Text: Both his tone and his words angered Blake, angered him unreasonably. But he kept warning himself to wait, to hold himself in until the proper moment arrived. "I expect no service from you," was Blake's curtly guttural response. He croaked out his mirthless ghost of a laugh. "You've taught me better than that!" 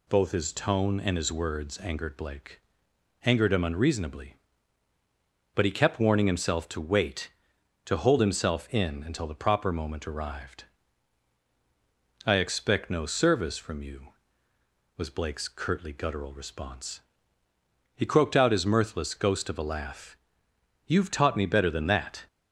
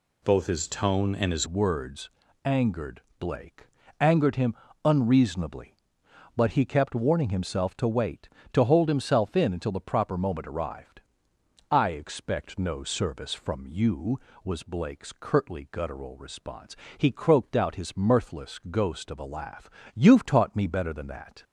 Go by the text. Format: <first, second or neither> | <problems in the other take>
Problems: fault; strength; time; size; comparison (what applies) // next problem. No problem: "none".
first | changes voice at "words"; from 1.4 s on; 20.0 s long // pauses between "words" and "angered"; slight; at 2.0 s; 0.36 s long // pauses between "angered" and "Blake"; slight; at 3.0 s; 0.18 s long // pauses between "him" and "unreasonably"; slight; at 4.5 s; 0.32 s long